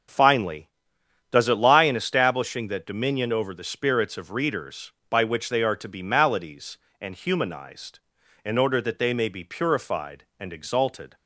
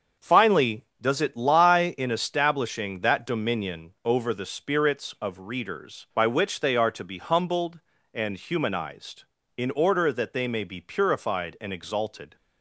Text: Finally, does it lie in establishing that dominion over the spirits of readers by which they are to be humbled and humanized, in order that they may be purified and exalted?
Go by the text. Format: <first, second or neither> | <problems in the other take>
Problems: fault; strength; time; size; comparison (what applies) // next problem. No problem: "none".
second | starts louder than the rest; until 1.7 s; 7 dB; also in the second // says "maladies" for "humbled"; at 6.0 s